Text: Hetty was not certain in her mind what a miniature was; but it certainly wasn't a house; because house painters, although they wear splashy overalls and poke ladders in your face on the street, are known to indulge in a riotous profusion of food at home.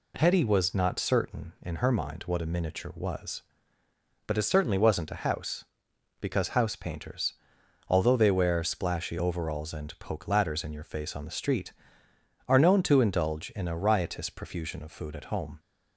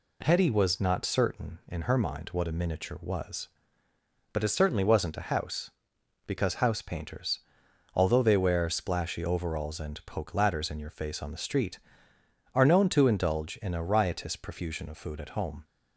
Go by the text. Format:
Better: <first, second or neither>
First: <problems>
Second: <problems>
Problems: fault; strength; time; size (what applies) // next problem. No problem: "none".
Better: neither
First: none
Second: none